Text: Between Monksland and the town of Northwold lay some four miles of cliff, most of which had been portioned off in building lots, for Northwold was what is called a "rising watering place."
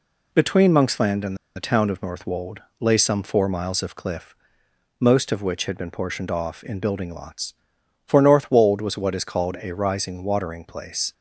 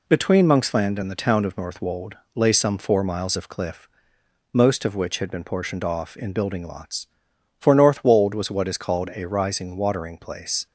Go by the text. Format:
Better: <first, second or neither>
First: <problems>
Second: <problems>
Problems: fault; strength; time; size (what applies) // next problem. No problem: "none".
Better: second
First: pauses between "and" and "the"; slight; at 1.3 s; 0.19 s long // pauses between "Northwold" and "lay"; slight; at 2.6 s; 0.20 s long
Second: pauses between "Northwold" and "lay"; slight; at 2.1 s; 0.20 s long